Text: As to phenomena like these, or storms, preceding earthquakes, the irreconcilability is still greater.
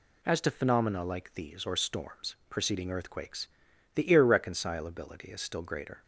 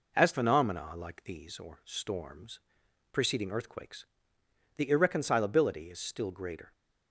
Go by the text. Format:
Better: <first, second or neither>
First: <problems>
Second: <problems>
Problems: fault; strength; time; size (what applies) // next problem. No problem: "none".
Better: first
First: none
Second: skips "to"; at 0.3 s